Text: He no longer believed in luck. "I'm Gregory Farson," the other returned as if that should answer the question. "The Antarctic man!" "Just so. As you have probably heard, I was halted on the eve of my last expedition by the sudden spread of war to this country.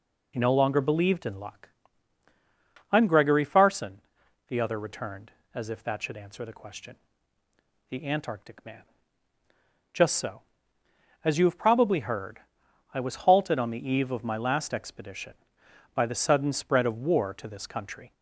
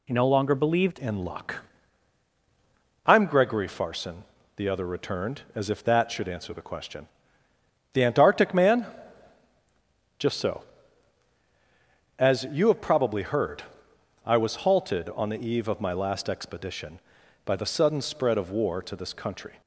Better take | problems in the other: first | changes voice at "in"; from 0.9 s on; 18.7 s long

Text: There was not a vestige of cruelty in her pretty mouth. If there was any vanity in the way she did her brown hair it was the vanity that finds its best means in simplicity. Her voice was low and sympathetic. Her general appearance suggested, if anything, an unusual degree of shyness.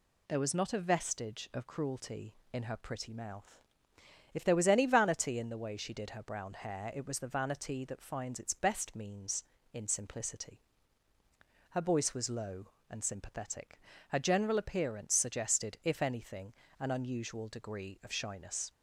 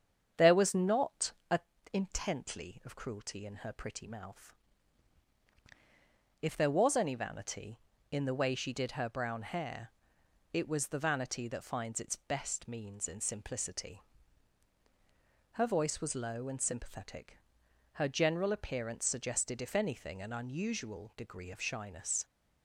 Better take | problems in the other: first | starts louder than the rest; strong; until 1.5 s; 8 dB // pauses between "not" and "a"; slight; at 1.3 s; 0.16 s long // says "intently" for "vestige"; at 1.9 s // pauses between "hair" and "it"; noticeable; at 9.9 s; 0.62 s long

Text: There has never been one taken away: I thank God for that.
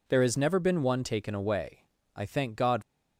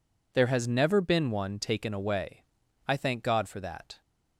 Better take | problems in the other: second | stops before "for that"; at 2.8 s

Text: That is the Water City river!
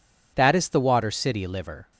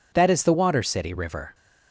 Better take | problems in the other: second | says "liver" for "river"; at 1.4 s

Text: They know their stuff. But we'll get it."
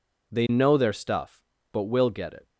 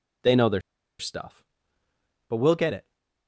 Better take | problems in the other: first | pauses between "their" and "stuff"; at 0.6 s; 0.38 s long

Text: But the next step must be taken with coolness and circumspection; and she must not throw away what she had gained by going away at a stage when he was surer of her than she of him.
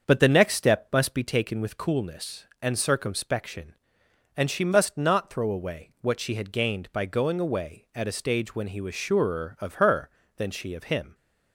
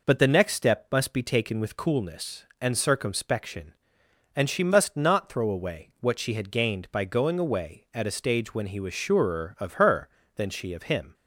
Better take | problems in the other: second | starts louder than the rest; until 1.2 s; 7 dB

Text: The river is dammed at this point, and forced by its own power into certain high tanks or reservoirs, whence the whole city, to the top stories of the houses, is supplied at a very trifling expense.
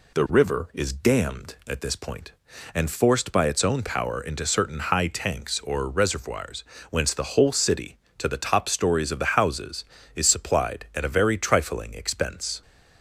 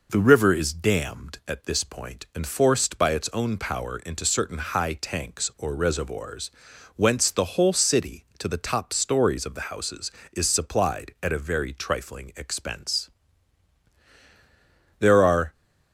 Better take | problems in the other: first | goes on to say "There are"; from 14.9 s on; 0.54 s long

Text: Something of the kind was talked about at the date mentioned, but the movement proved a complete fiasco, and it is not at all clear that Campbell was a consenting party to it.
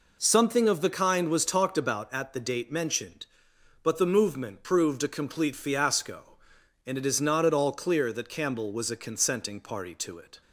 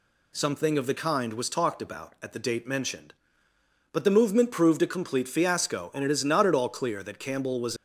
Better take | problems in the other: first | stops before "a consenting party to it"; at 7.7 s

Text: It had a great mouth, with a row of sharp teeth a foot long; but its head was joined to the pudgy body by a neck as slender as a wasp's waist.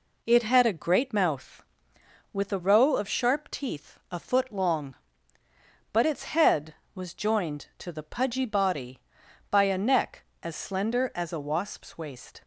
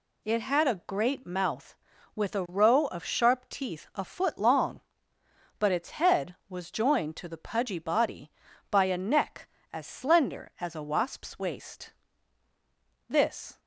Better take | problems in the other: first | goes on to say "This"; from 13.0 s on; 0.52 s long

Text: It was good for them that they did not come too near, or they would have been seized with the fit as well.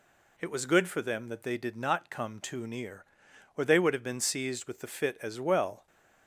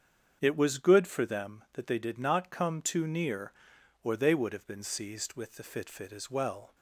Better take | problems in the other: first | starts louder than the rest; strong; until 1.4 s; 7.5 dB // says "fit" twice; at 5.8 s

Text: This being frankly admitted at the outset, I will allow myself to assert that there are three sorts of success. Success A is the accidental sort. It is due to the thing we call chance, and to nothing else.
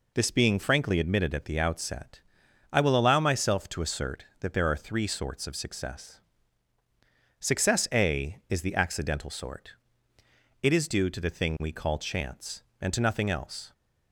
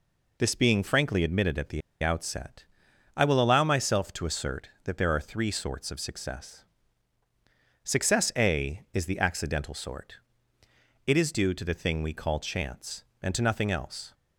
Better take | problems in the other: first | pauses between "the" and "outset"; slight; at 1.8 s; 0.22 s long

